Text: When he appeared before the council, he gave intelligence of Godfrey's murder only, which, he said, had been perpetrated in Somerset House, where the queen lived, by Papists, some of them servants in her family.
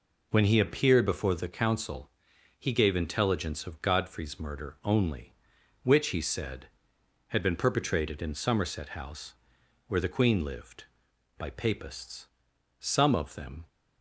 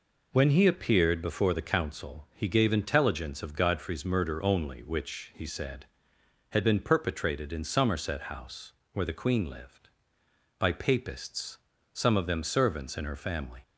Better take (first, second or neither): second